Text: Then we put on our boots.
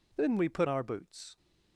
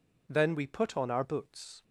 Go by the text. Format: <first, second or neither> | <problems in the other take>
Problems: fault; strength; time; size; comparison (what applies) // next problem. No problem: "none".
second | skips "on"; at 0.6 s